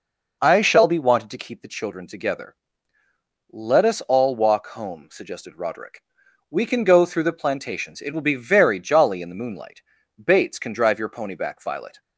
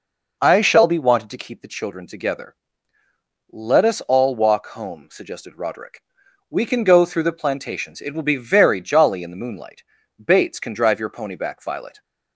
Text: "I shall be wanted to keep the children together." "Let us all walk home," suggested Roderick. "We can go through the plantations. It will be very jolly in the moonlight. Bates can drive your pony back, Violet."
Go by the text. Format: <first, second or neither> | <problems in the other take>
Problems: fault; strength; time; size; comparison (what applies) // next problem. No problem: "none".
neither | none